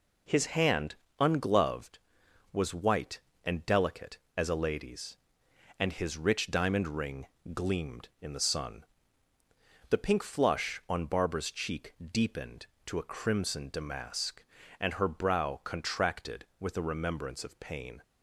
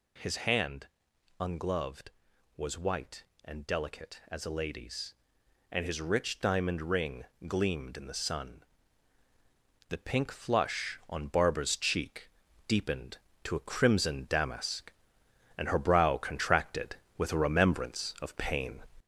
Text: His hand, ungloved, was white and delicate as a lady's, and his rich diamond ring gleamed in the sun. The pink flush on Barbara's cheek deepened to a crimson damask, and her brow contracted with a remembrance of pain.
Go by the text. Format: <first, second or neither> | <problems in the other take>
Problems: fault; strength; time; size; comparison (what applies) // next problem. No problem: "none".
first | gets louder; noticeable; throughout; 4.5 dB // pauses between "ring" and "gleamed"; slight; at 7.2 s; 0.22 s long; slight in the first // pauses between "cheek" and "deepened"; at 12.2 s; 0.38 s long; slight in the first